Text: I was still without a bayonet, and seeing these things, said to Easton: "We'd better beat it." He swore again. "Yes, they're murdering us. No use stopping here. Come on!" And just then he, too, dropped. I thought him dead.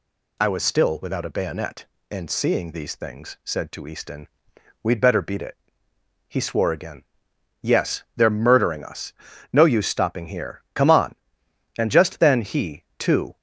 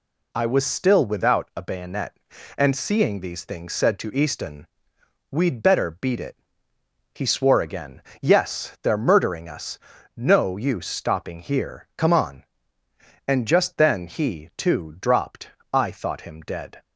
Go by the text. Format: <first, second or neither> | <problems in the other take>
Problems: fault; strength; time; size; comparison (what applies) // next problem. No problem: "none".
second | stops before "dropped I thought him dead"; at 13.3 s